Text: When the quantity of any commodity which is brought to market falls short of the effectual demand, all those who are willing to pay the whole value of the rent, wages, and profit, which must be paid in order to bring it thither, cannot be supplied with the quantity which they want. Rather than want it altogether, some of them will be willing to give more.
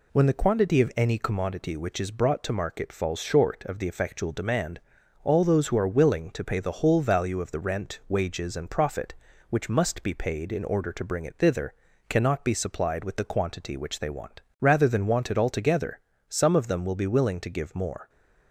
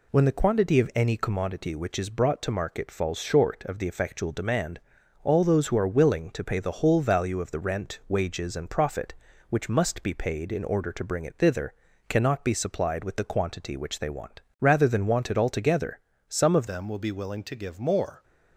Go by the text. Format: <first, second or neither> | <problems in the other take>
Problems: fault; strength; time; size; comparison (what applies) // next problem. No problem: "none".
first | changes voice at "them"; from 16.6 s on; 1.6 s long